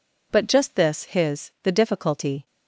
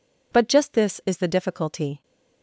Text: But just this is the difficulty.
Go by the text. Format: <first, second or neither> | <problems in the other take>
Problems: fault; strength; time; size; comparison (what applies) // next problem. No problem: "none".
second | says "his" for "is"; at 1.0 s